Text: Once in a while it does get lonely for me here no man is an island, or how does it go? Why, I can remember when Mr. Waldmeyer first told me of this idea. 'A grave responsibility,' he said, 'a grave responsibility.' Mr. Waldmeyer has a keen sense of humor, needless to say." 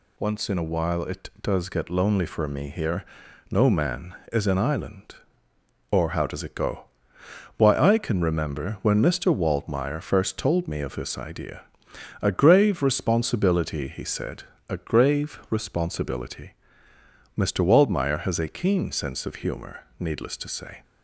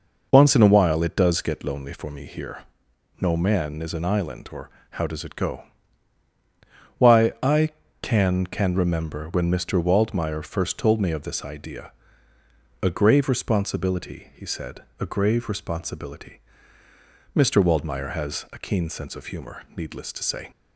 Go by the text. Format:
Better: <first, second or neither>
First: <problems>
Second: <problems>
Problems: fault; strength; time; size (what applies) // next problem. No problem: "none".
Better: first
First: pauses between "here" and "no"; noticeable; at 3.0 s; 0.46 s long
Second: pauses between "here" and "no"; noticeable; at 2.6 s; 0.60 s long // pauses between "or" and "how"; slight; at 4.7 s; 0.22 s long // says "can" twice; at 8.4 s